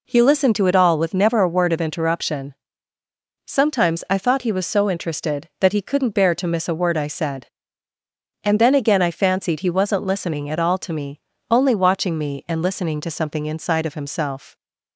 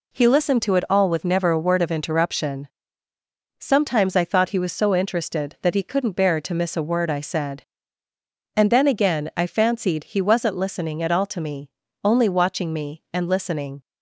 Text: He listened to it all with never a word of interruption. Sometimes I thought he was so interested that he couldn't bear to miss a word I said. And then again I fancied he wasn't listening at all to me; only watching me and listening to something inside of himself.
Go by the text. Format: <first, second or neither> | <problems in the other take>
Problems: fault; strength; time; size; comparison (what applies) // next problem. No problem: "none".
first | stops before "to something inside of himself"; at 13.8 s